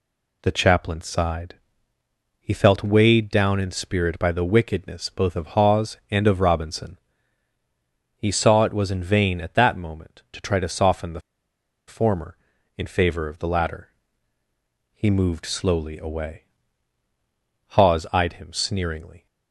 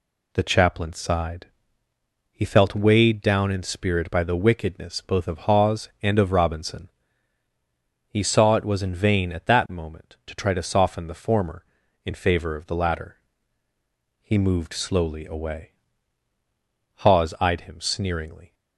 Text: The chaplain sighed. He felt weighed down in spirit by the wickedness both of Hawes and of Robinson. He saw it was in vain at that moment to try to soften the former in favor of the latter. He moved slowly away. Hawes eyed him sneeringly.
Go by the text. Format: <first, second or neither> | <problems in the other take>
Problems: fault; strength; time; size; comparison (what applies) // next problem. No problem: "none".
second | pauses between "the" and "former"; noticeable; at 11.1 s; 0.68 s long